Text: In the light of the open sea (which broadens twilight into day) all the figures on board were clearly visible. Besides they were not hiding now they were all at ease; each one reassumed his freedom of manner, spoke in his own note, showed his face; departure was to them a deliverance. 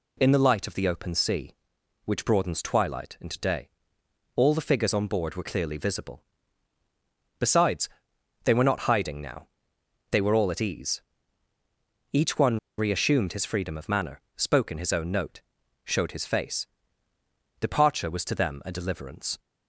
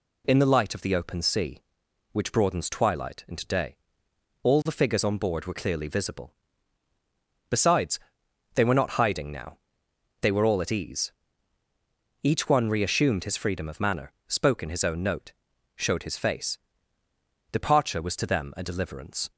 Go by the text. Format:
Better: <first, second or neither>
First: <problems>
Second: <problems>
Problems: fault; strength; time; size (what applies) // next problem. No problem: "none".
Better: second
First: pauses between "Besides" and "they"; noticeable; at 7.8 s; 0.54 s long // pauses between "now" and "they"; noticeable; at 9.4 s; 0.64 s long // pauses between "one" and "reassumed"; slight; at 12.5 s; 0.19 s long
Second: pauses between "Besides" and "they"; noticeable; at 7.9 s; 0.54 s long // pauses between "now" and "they"; noticeable; at 9.5 s; 0.64 s long